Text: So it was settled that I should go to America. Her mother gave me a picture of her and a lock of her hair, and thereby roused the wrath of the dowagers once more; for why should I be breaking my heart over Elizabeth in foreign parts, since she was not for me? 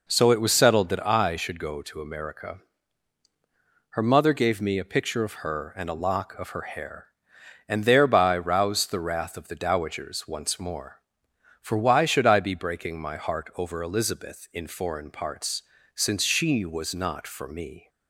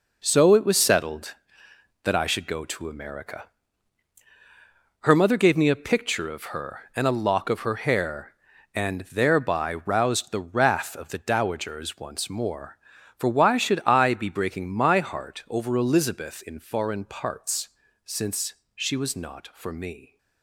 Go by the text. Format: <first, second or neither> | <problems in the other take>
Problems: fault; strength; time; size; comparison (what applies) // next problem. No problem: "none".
first | gets quieter; strong; throughout; 8.5 dB // pauses between "since" and "she"; slight; at 18.5 s; 0.22 s long